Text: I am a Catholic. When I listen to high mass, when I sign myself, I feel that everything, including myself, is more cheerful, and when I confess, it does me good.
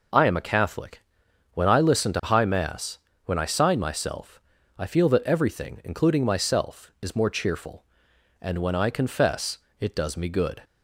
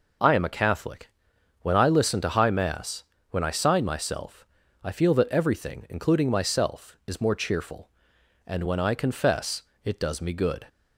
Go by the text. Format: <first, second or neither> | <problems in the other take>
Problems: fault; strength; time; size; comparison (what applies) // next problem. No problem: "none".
neither | none